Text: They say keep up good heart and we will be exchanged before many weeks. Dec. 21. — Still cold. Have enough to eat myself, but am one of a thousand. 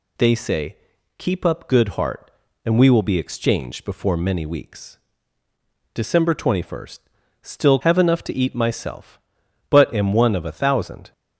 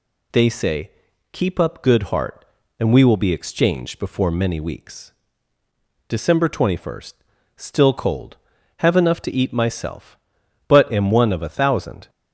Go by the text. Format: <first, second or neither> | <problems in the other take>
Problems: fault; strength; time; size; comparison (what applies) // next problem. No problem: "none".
second | pauses between "say" and "keep"; at 0.7 s; 0.42 s long; also in the second // skips "cold"; at 7.7 s